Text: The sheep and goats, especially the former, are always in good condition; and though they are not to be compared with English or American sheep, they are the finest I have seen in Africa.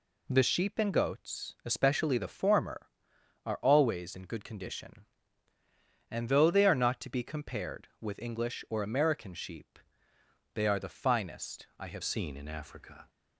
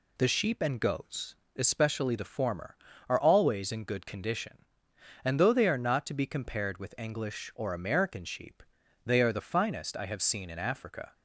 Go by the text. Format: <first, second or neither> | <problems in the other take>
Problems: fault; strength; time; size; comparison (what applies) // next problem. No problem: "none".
second | changes voice at "seen"; from 12.0 s on; 1.0 s long